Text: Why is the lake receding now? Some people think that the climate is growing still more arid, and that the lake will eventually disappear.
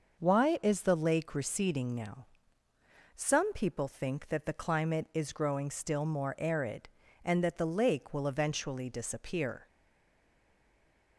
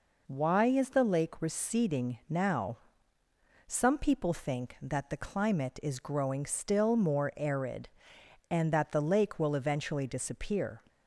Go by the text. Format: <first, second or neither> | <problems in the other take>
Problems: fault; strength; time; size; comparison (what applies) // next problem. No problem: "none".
second | stays silent after the last word; noticeable; from 9.6 s on; 1.5 s long